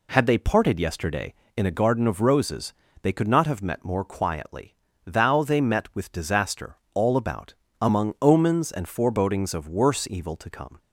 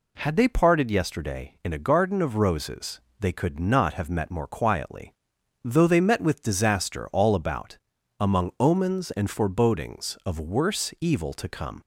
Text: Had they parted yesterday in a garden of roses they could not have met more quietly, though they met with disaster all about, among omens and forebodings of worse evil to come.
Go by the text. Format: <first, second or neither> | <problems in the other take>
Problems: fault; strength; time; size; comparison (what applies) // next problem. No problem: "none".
second | pauses between "roses" and "they"; slight; at 2.7 s; 0.28 s long; slight in the second // says "thou" for "though"; at 5.0 s // pauses between "disaster" and "all"; slight; at 6.7 s; 0.18 s long